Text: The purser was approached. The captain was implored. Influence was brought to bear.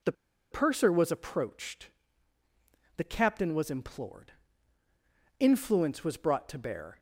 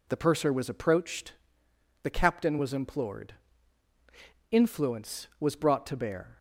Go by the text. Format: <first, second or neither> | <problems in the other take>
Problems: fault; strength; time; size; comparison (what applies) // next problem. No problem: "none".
second | pauses between "The" and "purser"; at 0.1 s; 0.38 s long